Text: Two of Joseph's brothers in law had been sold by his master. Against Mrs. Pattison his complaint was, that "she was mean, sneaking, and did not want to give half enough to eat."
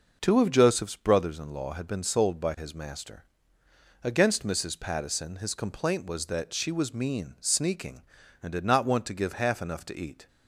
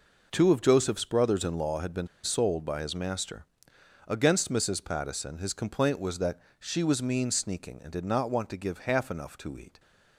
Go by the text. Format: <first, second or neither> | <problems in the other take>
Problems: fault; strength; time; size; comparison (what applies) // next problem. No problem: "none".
first | pauses between "been" and "sold"; slight; at 2.0 s; 0.15 s long // pauses between "that" and "she"; slight; at 6.3 s; 0.20 s long